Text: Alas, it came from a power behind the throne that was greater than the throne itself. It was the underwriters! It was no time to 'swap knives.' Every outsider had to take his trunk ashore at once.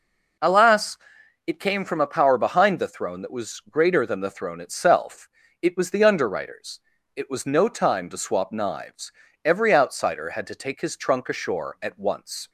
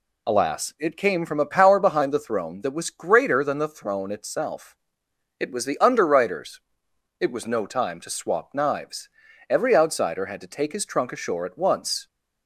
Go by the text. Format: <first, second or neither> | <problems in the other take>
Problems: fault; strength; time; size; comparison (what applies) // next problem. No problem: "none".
neither | none